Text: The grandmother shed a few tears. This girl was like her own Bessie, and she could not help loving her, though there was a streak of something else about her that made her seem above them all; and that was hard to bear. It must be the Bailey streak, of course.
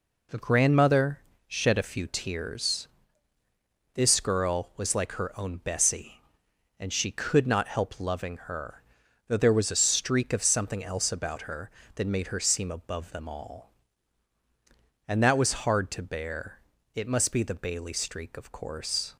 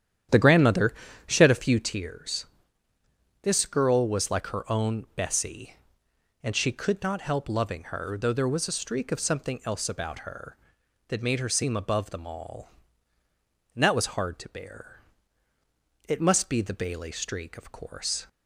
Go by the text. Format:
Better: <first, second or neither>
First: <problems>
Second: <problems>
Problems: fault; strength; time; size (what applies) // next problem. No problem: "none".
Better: first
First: pauses between "grandmother" and "shed"; slight; at 1.1 s; 0.30 s long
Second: starts louder than the rest; strong; until 2.1 s; 10 dB // pauses between "grandmother" and "shed"; slight; at 0.9 s; 0.32 s long